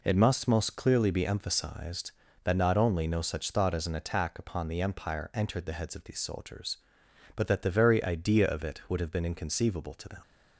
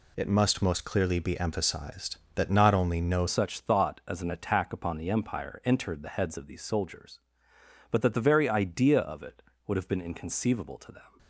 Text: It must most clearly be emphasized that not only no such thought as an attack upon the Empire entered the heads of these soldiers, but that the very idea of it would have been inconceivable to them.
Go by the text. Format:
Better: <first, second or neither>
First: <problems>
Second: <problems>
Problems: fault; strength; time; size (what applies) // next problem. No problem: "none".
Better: first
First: none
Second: changes voice at "such"; from 3.2 s on; 7.9 s long